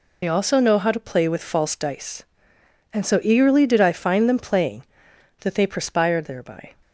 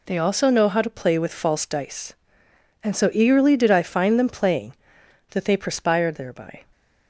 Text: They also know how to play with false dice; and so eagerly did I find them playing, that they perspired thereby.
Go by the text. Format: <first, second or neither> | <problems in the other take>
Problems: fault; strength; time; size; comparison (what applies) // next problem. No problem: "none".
second | loses the start of "They"; at 0.2 s; 60 ms